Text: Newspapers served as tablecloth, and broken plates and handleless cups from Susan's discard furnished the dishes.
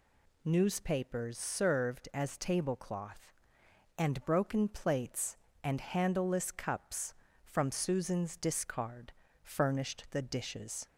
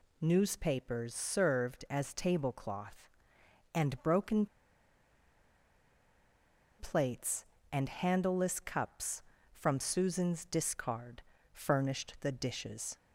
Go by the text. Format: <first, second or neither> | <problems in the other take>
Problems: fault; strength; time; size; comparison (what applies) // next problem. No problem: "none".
first | pauses between "broken" and "plates"; strong; at 4.4 s; 2.3 s long // pauses between "discard" and "furnished"; slight; at 11.2 s; 0.32 s long; slight in the first